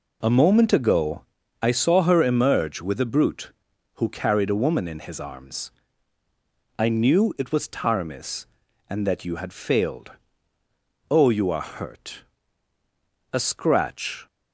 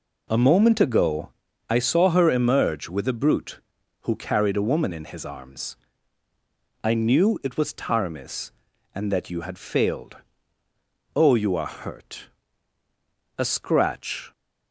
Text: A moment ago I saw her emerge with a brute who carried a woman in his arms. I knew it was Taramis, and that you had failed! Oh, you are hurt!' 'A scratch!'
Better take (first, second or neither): neither